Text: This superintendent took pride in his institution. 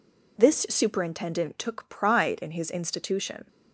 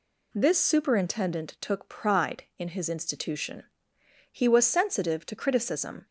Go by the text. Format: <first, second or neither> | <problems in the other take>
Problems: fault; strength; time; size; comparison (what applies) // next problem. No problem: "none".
first | goes on to say "He was sensitive to criticism"; strong; from 4.3 s on; 1.7 s long